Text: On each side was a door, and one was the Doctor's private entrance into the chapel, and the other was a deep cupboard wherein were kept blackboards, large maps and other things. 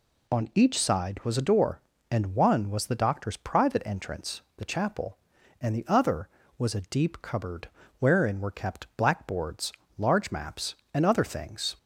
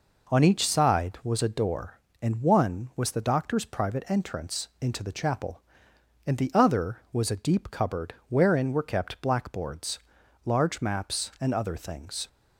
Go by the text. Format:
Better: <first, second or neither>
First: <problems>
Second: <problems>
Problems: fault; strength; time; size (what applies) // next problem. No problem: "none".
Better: second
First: skips "into"; at 4.4 s // pauses between "cupboard" and "wherein"; slight; at 7.6 s; 0.30 s long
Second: none